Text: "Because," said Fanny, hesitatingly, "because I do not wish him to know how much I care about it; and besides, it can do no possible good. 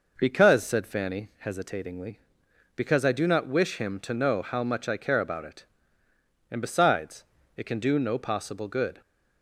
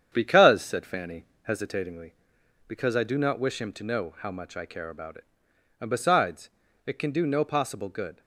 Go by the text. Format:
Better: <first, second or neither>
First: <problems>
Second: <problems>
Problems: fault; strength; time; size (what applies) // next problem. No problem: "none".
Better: first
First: none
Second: gets quieter; noticeable; throughout; 4 dB